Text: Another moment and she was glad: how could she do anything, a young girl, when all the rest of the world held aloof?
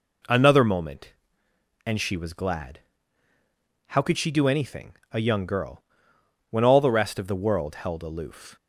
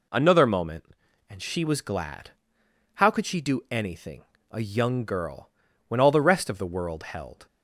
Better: first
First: none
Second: stops before "aloof"; at 7.4 s

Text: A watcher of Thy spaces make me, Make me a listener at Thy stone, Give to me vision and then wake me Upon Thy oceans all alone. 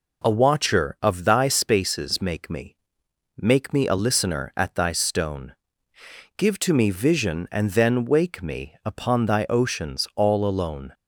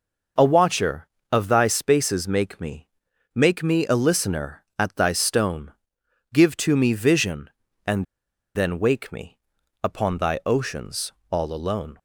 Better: first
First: none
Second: pauses between "and" and "then"; noticeable; at 8.0 s; 0.51 s long // pauses between "me" and "Upon"; noticeable; at 9.3 s; 0.46 s long // pauses between "oceans" and "all"; slight; at 11.1 s; 0.20 s long

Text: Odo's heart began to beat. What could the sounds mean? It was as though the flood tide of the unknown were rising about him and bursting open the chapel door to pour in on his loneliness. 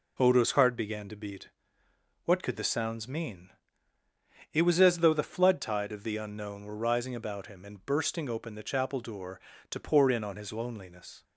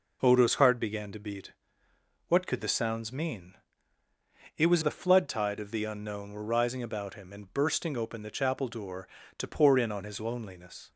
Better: first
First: none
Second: skips "as though"; at 4.8 s

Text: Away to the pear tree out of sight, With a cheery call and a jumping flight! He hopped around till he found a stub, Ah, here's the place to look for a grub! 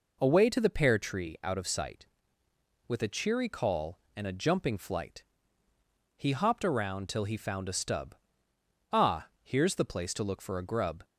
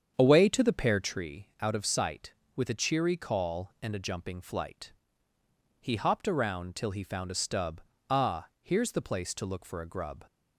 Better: first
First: none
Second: starts louder than the rest; strong; until 1.3 s; 8 dB

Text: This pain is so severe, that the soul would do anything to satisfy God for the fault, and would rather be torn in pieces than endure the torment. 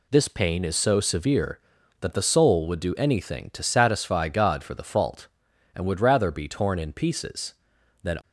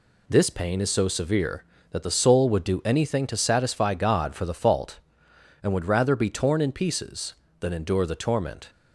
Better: second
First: stops before "endure the torment"; at 8.2 s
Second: none

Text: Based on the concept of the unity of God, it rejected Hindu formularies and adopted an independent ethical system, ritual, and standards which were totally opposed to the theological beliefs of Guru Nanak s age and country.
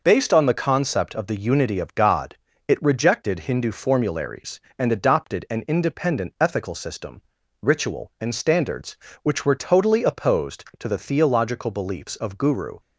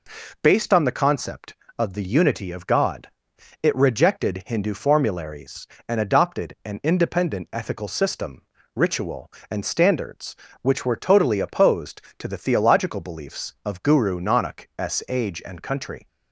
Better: second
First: stops before "Nanak s age and country"; at 12.7 s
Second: none

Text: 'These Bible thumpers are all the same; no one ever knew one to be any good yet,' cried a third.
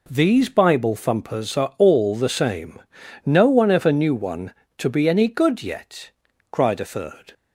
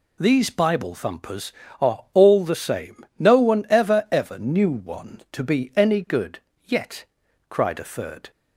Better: first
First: none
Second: says "ever" twice; at 4.1 s // pauses between "good" and "yet"; slight; at 6.3 s; 0.26 s long

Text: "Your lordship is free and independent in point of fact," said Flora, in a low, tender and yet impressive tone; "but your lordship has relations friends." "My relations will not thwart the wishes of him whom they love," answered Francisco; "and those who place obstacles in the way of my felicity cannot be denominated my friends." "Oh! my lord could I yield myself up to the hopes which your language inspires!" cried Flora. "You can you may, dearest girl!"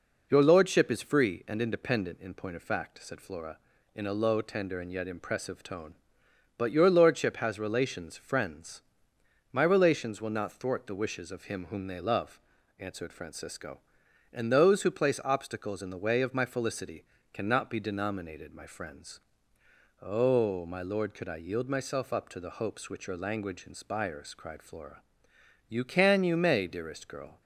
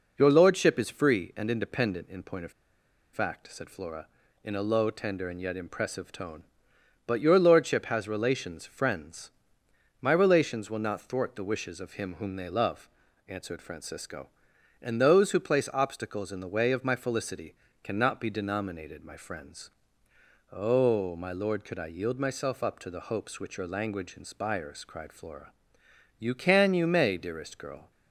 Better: first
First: pauses between "felicity" and "cannot"; slight; at 17.0 s; 0.28 s long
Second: pauses between "of" and "fact"; noticeable; at 2.5 s; 0.62 s long // pauses between "felicity" and "cannot"; slight; at 17.5 s; 0.28 s long

